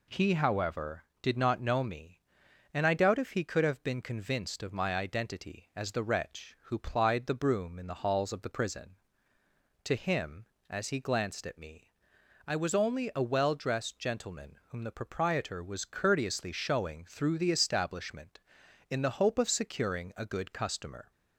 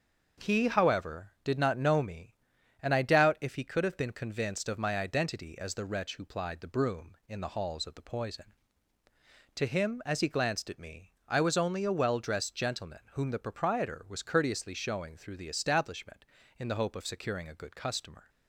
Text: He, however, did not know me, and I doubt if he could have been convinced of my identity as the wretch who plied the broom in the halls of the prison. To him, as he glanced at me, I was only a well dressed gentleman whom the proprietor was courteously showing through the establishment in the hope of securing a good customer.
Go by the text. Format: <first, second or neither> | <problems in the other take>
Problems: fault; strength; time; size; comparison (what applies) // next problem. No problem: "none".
first | starts louder than the rest; until 1.5 s; 6.5 dB // says "poison" for "prison"; at 8.0 s